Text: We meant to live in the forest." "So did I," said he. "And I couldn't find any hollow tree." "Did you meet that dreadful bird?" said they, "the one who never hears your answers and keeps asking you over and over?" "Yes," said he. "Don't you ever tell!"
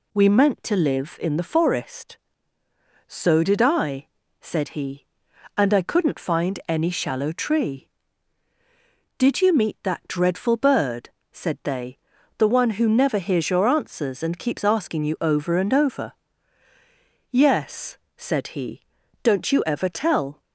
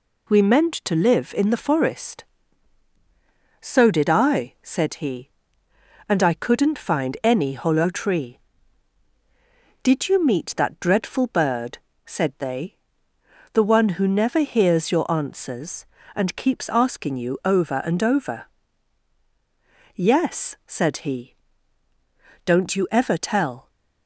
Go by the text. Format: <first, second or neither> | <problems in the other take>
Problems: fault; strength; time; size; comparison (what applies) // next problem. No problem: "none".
second | says "shallow" for "hollow"; at 6.8 s